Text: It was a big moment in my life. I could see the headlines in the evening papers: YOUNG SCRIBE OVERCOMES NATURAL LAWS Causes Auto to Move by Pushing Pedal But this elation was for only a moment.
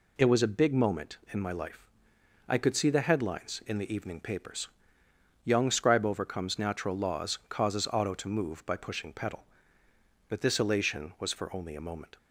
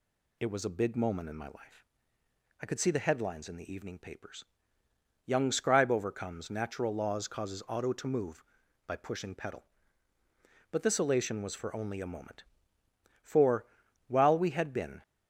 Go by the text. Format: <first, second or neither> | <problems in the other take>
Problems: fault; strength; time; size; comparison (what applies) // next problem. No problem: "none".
first | goes on to say "For while we had been"; strong; from 13.2 s on; 1.7 s long